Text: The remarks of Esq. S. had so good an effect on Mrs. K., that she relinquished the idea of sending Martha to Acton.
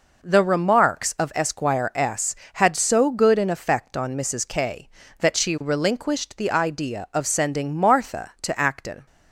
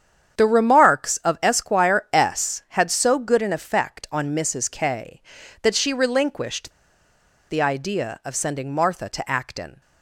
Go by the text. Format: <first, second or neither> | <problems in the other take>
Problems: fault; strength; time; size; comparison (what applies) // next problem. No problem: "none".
first | starts louder than the rest; strong; until 1.4 s; 8.5 dB // pauses between "relinquished" and "the"; noticeable; at 6.7 s; 0.79 s long